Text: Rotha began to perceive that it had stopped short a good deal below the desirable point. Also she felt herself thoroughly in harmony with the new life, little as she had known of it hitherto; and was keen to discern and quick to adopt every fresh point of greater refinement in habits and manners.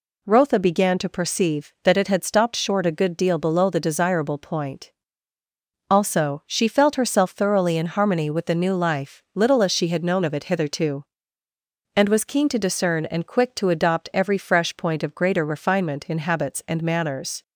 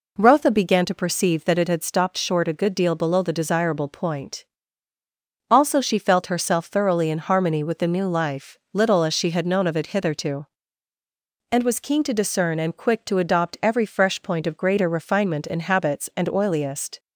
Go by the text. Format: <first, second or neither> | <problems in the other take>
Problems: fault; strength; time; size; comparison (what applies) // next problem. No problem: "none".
first | says "oiliest" for "manners"; at 16.2 s